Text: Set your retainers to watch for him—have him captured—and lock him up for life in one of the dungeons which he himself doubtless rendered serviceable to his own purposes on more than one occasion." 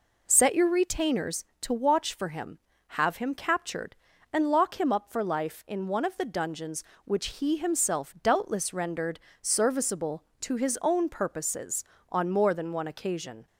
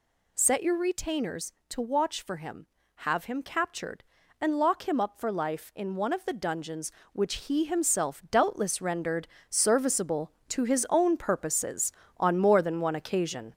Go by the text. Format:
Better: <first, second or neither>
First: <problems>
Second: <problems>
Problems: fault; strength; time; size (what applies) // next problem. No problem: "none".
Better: first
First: pauses between "rendered" and "serviceable"; slight; at 9.2 s; 0.20 s long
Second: gets louder; noticeable; throughout; 4.5 dB // pauses between "rendered" and "serviceable"; slight; at 9.2 s; 0.20 s long